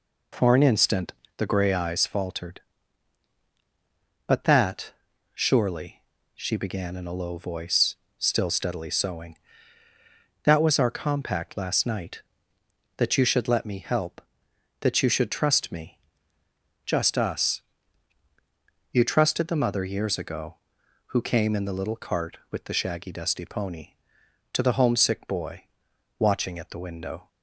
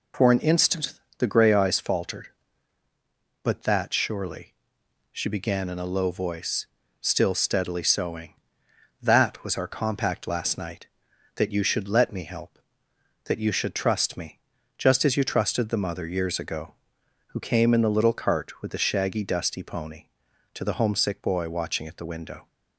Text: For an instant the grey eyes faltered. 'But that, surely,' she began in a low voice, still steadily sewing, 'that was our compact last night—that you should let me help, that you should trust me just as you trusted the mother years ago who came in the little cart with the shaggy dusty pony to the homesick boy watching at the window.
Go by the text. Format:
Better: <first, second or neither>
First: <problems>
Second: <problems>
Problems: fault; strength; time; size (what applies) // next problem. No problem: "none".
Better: second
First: pauses between "instant" and "the"; slight; at 1.1 s; 0.24 s long // pauses between "me" and "just"; noticeable; at 15.9 s; 0.86 s long // says "us" for "as"; at 17.1 s // pauses between "boy" and "watching"; noticeable; at 25.6 s; 0.56 s long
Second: pauses between "instant" and "the"; slight; at 0.9 s; 0.24 s long // pauses between "me" and "just"; at 14.3 s; 0.38 s long